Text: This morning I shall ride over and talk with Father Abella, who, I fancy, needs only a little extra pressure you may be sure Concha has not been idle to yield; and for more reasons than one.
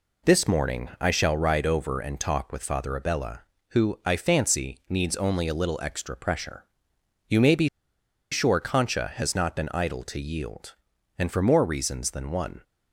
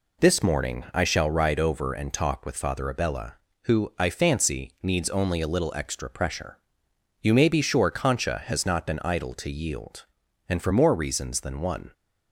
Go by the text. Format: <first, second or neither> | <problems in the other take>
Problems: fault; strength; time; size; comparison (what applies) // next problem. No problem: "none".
second | pauses between "pressure" and "you"; noticeable; at 6.6 s; 0.64 s long; noticeable in the second // pauses between "be" and "sure"; noticeable; at 7.6 s; 0.63 s long